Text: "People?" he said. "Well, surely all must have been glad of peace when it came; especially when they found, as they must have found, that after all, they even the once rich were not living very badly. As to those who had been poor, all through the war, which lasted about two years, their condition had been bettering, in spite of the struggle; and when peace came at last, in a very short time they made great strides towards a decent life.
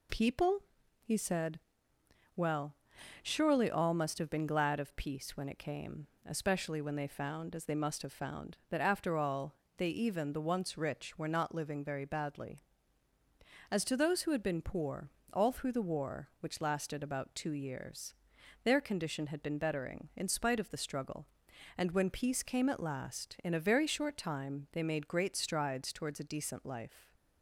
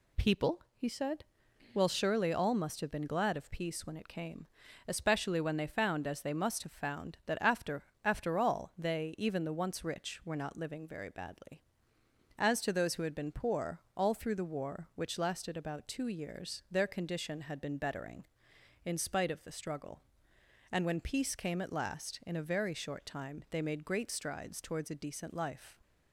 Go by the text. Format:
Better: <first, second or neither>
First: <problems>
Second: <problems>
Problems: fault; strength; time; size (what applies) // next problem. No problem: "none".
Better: first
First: none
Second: says "after" twice; at 8.0 s